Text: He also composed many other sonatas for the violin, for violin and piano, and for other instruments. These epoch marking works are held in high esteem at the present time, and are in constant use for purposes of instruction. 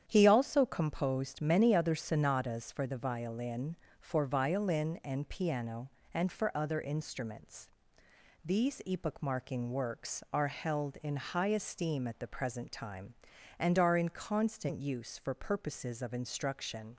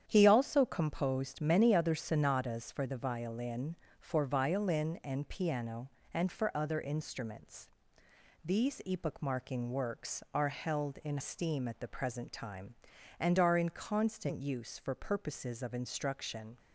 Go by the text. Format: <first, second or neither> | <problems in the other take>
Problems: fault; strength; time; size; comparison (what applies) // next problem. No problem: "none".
first | starts louder than the rest; strong; until 1.0 s; 9 dB; strong in the first // skips "high"; at 11.1 s